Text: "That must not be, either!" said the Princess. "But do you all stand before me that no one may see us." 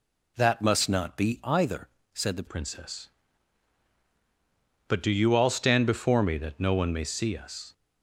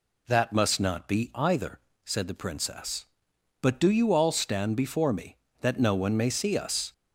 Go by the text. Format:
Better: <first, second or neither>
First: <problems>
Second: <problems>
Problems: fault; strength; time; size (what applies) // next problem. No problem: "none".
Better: second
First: changes voice at "Princess"; from 2.4 s on; 5.3 s long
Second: none